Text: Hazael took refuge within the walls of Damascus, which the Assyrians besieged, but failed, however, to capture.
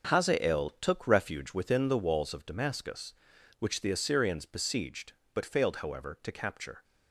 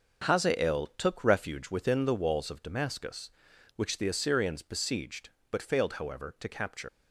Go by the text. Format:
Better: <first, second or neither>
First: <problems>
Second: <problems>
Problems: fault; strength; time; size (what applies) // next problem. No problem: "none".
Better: first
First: starts louder than the rest; until 1.1 s; 7 dB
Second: starts louder than the rest; until 1.3 s; 6.5 dB // leaves "capture" unfinished; at 6.8 s; 120 ms